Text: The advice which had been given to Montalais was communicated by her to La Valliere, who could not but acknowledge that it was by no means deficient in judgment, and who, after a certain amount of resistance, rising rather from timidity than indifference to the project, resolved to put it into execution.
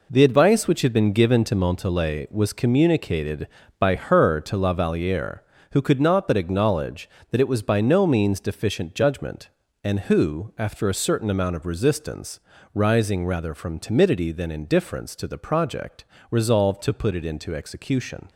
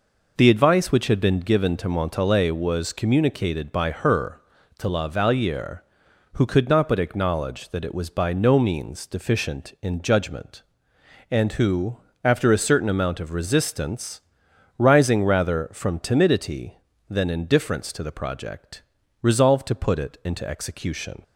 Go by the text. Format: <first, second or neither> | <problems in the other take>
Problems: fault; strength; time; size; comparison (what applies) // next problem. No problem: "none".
second | skips "in"; at 8.9 s